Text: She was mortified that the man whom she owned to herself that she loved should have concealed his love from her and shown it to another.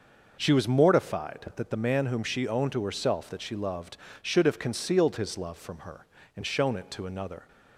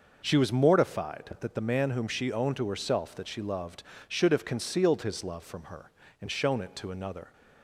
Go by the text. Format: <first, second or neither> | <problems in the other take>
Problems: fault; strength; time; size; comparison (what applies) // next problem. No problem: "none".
neither | none